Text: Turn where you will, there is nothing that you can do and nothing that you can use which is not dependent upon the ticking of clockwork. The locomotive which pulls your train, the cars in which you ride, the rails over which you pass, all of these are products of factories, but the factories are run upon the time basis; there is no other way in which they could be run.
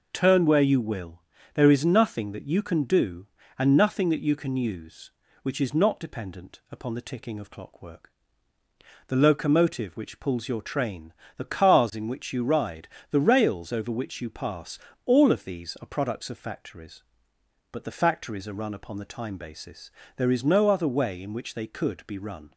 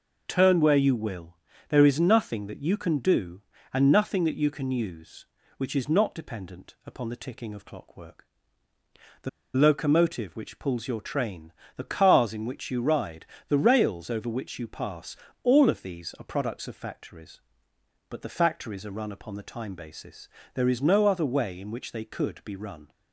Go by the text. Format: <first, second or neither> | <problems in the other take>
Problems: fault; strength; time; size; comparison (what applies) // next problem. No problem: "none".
first | pauses between "The" and "locomotive"; slight; at 9.2 s; 0.24 s long